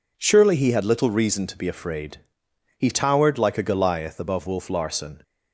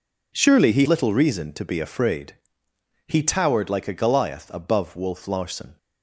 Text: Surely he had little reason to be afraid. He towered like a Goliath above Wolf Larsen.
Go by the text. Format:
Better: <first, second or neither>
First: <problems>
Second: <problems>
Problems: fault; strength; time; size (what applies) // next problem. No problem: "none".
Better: first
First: none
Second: skips "had"; at 0.8 s